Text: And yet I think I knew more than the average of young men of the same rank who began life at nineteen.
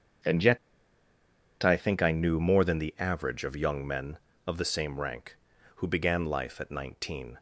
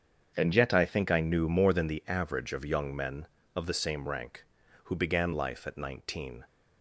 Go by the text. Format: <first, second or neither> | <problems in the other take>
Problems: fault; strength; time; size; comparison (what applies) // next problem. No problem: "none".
second | starts louder than the rest; strong; until 2.3 s; 7.5 dB; strong in the second // pauses between "yet" and "I"; at 0.5 s; 1.0 s long